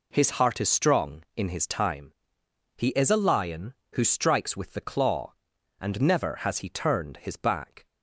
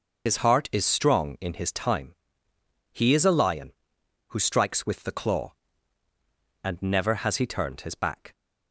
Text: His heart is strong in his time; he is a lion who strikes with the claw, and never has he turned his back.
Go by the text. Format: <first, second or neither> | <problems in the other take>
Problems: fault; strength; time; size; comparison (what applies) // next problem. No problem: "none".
first | loses the start of "His"; at 0.2 s; 65 ms